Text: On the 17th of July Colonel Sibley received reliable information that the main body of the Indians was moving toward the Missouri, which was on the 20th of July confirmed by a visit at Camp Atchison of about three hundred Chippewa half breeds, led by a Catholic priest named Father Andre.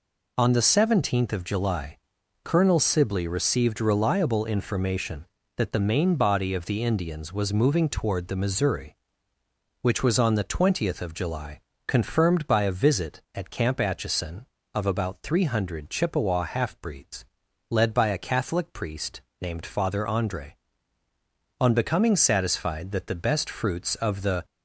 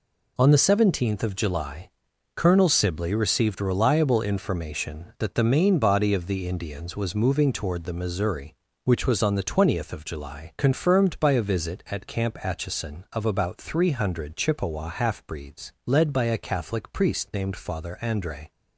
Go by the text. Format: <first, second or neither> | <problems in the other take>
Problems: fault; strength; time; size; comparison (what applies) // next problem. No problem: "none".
second | pauses between "July" and "Colonel"; noticeable; at 1.9 s; 0.48 s long; noticeable in the second // pauses between "July" and "confirmed"; slight; at 11.5 s; 0.28 s long // pauses between "priest" and "named"; slight; at 19.2 s; 0.20 s long // goes on to say "On becoming satisfied that the best fruits of the"; strong; from 21.5 s on; 2.8 s long